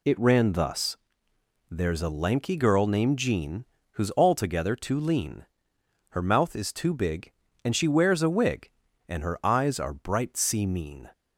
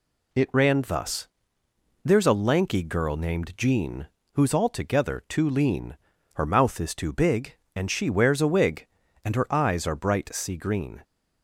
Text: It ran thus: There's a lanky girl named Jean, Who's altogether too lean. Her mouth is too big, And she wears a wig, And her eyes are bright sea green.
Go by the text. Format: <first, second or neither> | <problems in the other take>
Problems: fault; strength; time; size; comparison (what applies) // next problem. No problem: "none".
second | says "mean" for "green"; at 10.6 s